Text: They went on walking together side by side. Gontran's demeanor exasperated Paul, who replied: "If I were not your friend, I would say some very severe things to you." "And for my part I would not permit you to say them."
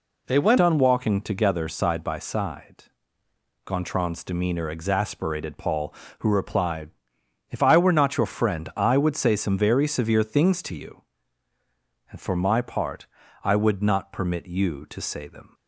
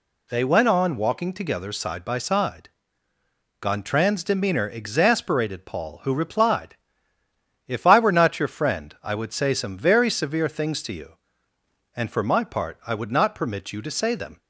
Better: second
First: changes voice at "on"; from 0.5 s on; 15.0 s long // pauses between "part" and "I"; at 13.0 s; 0.38 s long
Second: none

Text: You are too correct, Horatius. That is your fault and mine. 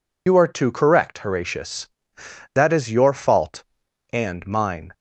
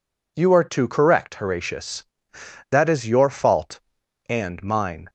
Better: second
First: loses the start of "You"; at 0.2 s; 65 ms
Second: none

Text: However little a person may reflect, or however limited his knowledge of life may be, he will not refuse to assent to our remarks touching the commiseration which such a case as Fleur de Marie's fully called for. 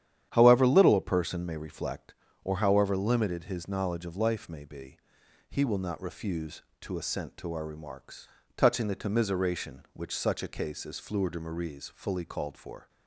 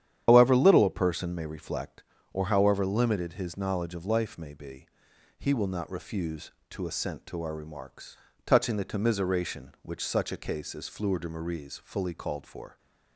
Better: first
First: starts louder than the rest; strong; until 1.3 s; 10 dB // pauses between "remarks" and "touching"; slight; at 8.2 s; 0.26 s long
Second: loses the start of "However"; at 0.2 s; 80 ms // starts louder than the rest; strong; until 1.2 s; 10 dB // pauses between "remarks" and "touching"; slight; at 8.1 s; 0.26 s long

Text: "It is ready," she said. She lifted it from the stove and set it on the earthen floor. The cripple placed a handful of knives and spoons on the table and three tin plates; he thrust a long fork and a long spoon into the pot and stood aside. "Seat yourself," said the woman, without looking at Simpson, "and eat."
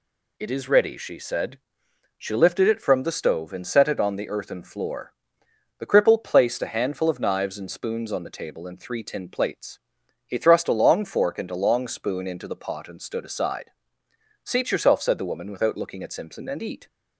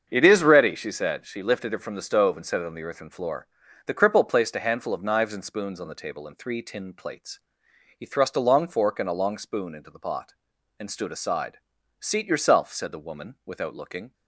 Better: first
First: none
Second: starts louder than the rest; until 1.1 s; 7 dB // stops before "at Simpson and eat"; at 14.1 s

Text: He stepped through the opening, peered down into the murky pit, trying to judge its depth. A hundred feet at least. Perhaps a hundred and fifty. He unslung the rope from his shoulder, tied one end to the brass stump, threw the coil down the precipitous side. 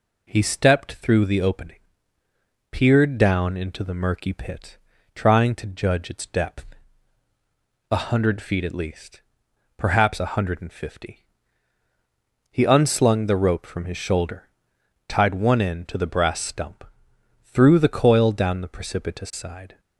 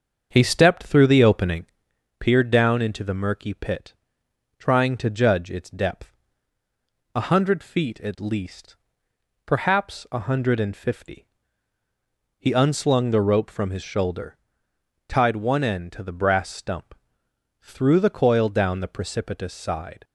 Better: first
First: none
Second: starts louder than the rest; strong; until 2.0 s; 7 dB

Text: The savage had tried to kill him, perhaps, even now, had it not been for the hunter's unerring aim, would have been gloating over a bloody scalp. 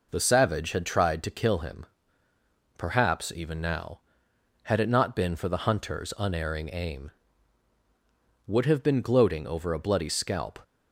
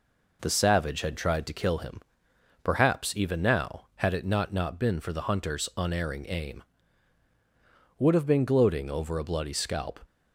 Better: first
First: none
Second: says "not" twice; at 4.5 s

